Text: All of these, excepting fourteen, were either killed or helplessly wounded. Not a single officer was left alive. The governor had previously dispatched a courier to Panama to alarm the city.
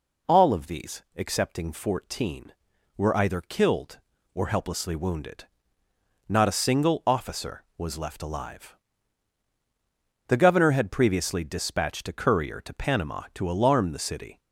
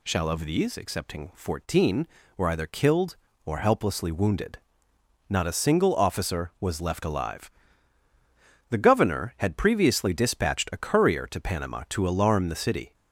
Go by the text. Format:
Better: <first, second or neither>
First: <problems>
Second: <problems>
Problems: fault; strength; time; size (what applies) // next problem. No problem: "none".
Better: first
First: none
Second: says "Shall" for "All"; at 0.0 s